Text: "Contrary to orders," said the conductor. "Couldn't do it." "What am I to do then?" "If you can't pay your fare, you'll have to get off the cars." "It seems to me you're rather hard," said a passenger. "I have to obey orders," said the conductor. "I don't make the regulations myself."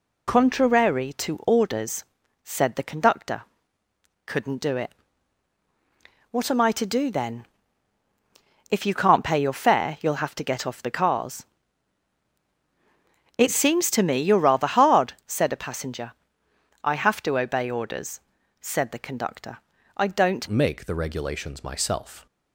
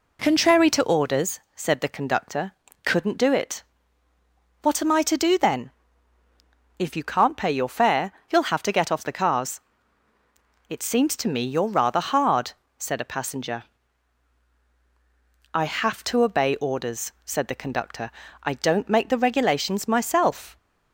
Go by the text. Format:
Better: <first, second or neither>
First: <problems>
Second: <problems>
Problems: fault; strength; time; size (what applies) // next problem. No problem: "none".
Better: second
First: changes voice at "make"; from 20.4 s on; 1.8 s long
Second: none